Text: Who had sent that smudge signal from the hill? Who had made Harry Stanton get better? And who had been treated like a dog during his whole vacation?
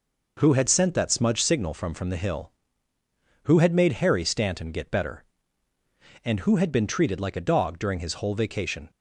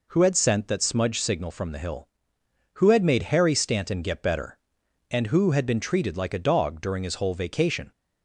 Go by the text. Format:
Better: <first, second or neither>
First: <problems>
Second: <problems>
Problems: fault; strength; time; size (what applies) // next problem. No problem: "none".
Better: second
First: says "from" twice; at 1.9 s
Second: none